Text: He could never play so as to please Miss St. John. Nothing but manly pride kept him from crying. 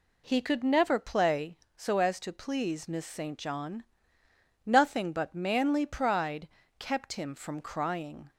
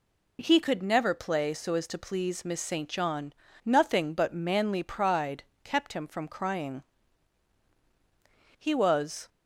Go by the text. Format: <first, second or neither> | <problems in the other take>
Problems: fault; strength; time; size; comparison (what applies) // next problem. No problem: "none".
first | pauses between "pride" and "kept"; slight; at 5.4 s; 0.22 s long; slight in the first // goes on to say "He was"; noticeable; from 8.5 s on; 0.70 s long